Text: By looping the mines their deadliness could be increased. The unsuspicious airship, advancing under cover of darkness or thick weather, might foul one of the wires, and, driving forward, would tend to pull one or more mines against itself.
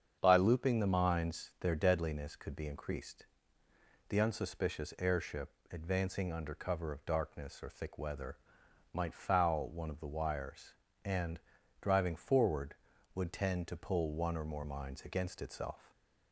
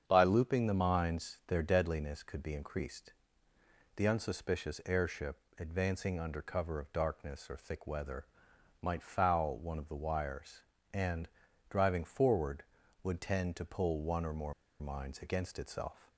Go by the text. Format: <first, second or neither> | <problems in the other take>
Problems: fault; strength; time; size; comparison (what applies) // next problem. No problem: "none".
first | starts louder than the rest; strong; until 1.1 s; 7.5 dB; strong in the first // pauses between "more" and "mines"; slight; at 14.5 s; 0.26 s long